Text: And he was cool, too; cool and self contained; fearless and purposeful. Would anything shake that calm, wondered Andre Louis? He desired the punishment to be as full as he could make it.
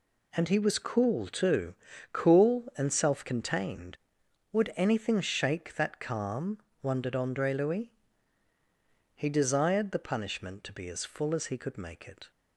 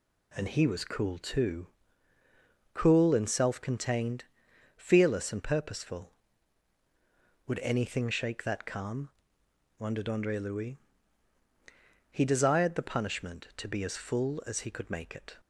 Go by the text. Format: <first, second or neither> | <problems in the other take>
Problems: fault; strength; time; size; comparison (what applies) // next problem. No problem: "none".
second | skips "fearless and purposeful"; at 4.2 s